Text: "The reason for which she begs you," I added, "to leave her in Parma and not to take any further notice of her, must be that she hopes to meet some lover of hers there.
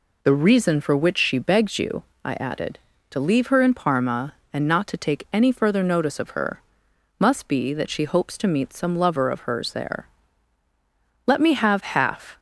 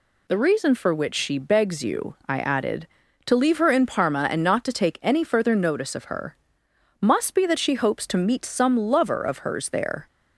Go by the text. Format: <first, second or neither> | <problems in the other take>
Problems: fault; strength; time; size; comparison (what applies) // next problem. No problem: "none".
second | goes on to say "Let me have half"; noticeable; from 11.2 s on; 1.1 s long